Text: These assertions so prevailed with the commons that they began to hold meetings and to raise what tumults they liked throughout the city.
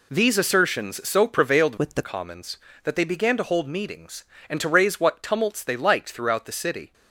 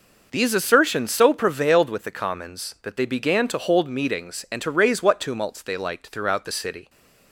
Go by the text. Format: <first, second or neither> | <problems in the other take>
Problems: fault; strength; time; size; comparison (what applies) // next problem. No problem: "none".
second | changes voice from "with" to "the"; from 1.7 to 2.0 s; 0.3 s long